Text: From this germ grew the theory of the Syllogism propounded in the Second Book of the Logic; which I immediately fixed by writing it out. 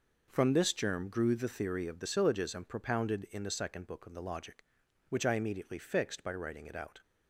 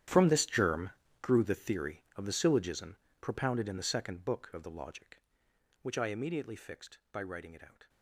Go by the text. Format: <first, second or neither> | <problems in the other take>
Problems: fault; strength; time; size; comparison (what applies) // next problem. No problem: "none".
first | gets quieter; strong; throughout; 18 dB // pauses between "germ" and "grew"; slight; at 0.8 s; 0.32 s long // pauses between "Syllogism" and "propounded"; slight; at 2.9 s; 0.24 s long